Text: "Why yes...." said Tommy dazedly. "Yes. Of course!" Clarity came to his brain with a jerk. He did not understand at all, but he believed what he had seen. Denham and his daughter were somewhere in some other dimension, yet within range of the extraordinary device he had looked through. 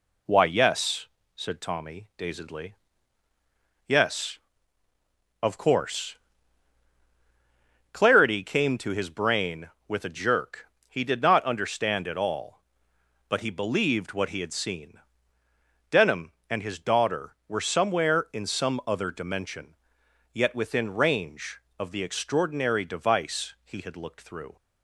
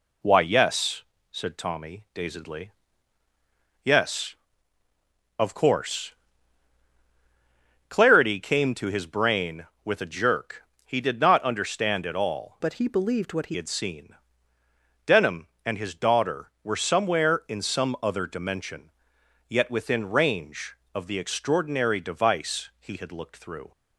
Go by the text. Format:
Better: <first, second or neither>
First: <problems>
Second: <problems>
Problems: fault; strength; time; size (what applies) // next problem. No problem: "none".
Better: first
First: none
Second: changes voice from "but" to "he"; from 12.6 to 13.5 s; 0.9 s long